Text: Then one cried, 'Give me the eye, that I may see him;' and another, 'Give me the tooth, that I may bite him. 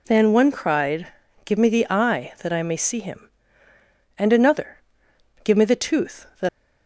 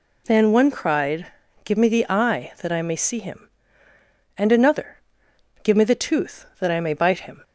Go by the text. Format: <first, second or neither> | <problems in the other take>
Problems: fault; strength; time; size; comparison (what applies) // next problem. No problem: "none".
second | stops before "I may bite him"; at 6.4 s